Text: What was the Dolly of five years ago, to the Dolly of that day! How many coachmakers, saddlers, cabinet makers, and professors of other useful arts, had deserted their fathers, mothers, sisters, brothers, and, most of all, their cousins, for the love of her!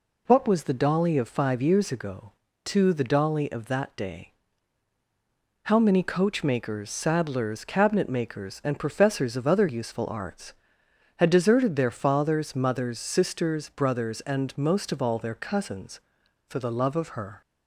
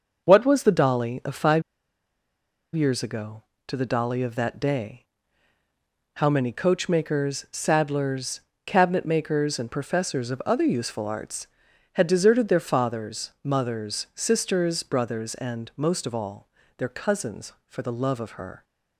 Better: first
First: none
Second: starts louder than the rest; noticeable; until 1.2 s; 6 dB // pauses between "five" and "years"; at 1.6 s; 1.1 s long

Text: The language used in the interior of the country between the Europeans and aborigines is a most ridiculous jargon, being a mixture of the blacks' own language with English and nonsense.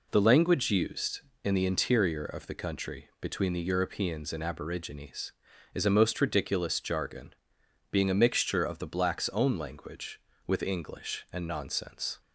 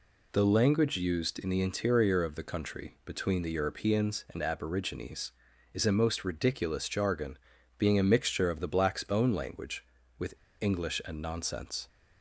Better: first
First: none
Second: pauses between "with" and "English"; slight; at 10.3 s; 0.23 s long

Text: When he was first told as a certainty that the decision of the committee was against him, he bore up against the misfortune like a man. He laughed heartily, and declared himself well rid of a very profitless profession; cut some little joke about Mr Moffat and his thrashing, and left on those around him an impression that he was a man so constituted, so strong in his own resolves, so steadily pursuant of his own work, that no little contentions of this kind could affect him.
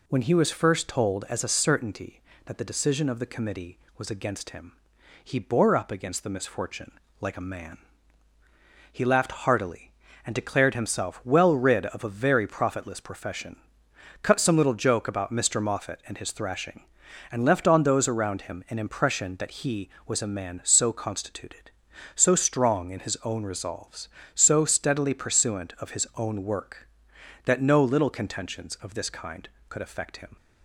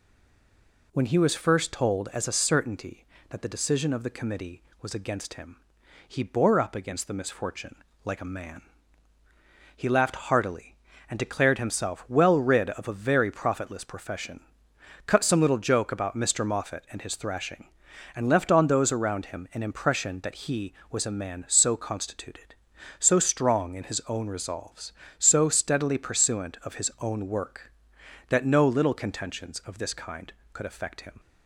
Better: first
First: pauses between "misfortune" and "like"; slight; at 6.9 s; 0.28 s long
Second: stays silent before the first word; slight; until 0.9 s; 0.9 s long // pauses between "misfortune" and "like"; slight; at 7.7 s; 0.28 s long

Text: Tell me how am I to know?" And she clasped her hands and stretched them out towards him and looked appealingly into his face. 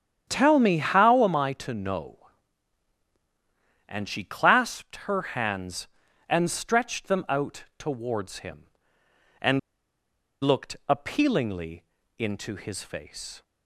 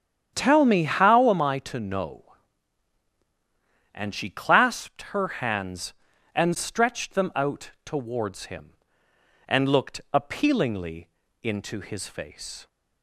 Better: second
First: starts louder than the rest; strong; until 1.3 s; 9 dB // pauses between "and" and "looked"; noticeable; at 9.5 s; 0.84 s long // pauses between "appealingly" and "into"; slight; at 11.8 s; 0.34 s long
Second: starts louder than the rest; strong; until 1.3 s; 8.5 dB // pauses between "appealingly" and "into"; slight; at 11.0 s; 0.34 s long

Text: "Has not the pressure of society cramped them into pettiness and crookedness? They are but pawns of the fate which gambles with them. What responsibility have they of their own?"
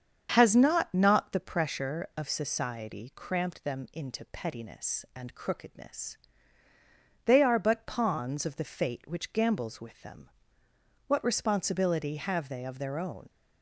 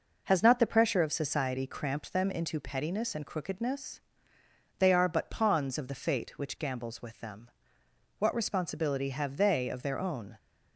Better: second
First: starts louder than the rest; strong; until 1.3 s; 7.5 dB // says "not" twice; at 0.9 s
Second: none

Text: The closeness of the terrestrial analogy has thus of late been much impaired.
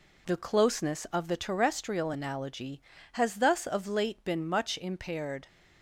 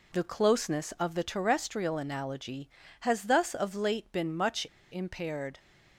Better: first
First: none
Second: pauses between "much" and "impaired"; slight; at 4.6 s; 0.26 s long

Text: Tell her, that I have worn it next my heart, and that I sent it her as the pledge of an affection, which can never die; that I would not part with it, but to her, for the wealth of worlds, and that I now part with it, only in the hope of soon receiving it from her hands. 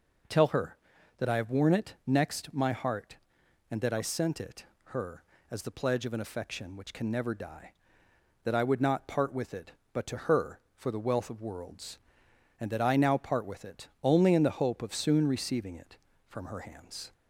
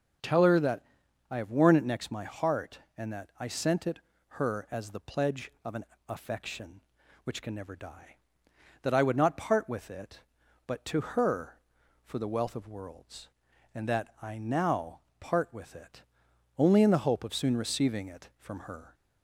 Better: first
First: pauses between "it" and "her"; slight; at 4.6 s; 0.20 s long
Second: starts louder than the rest; until 1.7 s; 6.5 dB // pauses between "that" and "I"; noticeable; at 0.8 s; 0.48 s long // pauses between "it" and "her"; slight; at 3.9 s; 0.30 s long // pauses between "an" and "affection"; slight; at 5.8 s; 0.24 s long // pauses between "now" and "part"; slight; at 14.9 s; 0.20 s long // stops before "hands"; at 18.9 s

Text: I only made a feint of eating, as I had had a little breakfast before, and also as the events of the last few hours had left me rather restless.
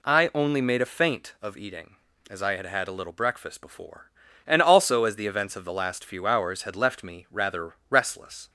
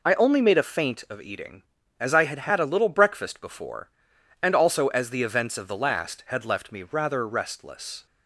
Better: first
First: none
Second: skips "few hours"; at 6.2 s

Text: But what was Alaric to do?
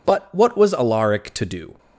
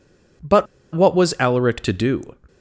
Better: first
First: none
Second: pauses between "But" and "what"; slight; at 0.6 s; 0.29 s long

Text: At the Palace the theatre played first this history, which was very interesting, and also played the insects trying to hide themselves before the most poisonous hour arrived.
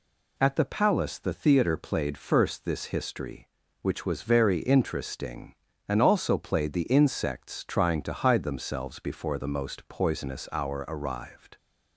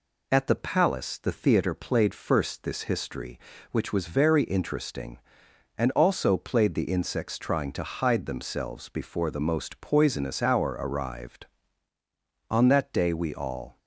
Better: first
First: none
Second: goes on to say "On that day we all"; noticeable; from 12.5 s on; 1.2 s long

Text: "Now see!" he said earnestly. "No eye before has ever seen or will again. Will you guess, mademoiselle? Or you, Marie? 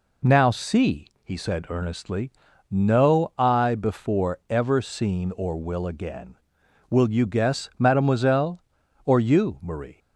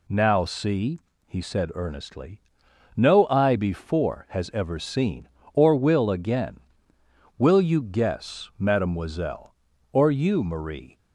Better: second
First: skips "has"; at 4.4 s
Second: none

